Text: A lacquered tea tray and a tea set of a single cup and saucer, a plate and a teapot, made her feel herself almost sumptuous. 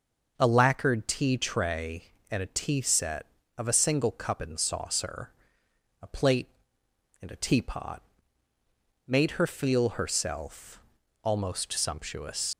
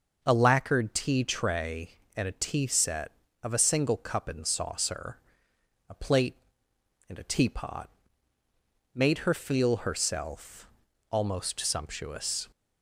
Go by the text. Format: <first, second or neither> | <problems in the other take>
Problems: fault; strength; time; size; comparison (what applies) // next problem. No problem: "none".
second | pauses between "herself" and "almost"; at 10.8 s; 0.42 s long; also in the second // leaves "sumptuous" unfinished; at 12.5 s; 100 ms